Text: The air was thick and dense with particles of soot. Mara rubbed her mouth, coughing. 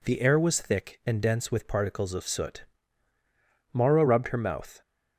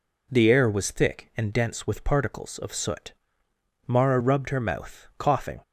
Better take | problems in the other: second | stops before "coughing"; at 4.8 s

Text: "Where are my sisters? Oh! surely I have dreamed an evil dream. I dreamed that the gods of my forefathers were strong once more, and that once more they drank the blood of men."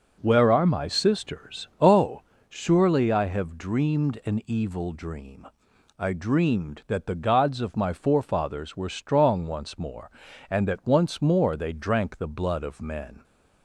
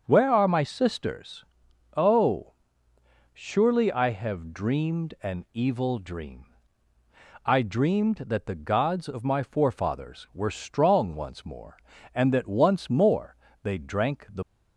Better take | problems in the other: first | starts louder than the rest; until 1.0 s; 6.5 dB; also in the first // pauses between "more" and "they"; slight; at 13.3 s; 0.26 s long // stops before "blood of men"; at 14.4 s

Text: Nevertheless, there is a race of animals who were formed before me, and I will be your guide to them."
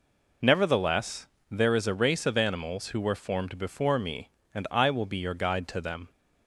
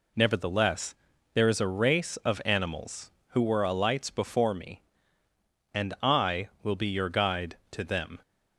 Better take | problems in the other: first | says "alights" for "formed"; at 3.6 s

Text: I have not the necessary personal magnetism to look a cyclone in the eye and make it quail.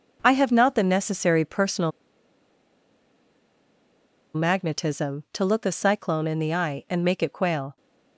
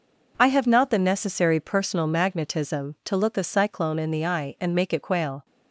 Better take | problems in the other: second | pauses between "personal" and "magnetism"; strong; at 1.9 s; 2.4 s long

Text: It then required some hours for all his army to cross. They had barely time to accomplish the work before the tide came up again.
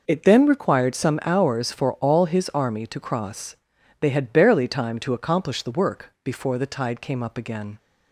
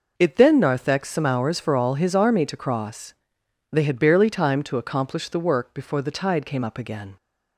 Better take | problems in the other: first | says "narthex" for "required"; at 0.5 s

